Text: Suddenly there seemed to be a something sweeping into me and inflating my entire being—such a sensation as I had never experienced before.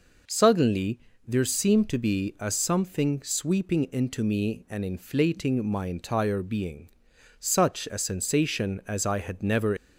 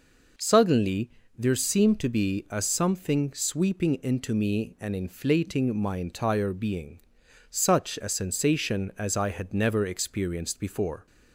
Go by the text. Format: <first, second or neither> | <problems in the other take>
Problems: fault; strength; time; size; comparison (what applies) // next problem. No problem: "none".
second | pauses between "Suddenly" and "there"; slight; at 0.9 s; 0.28 s long; slight in the second // stops before "experienced before"; at 9.7 s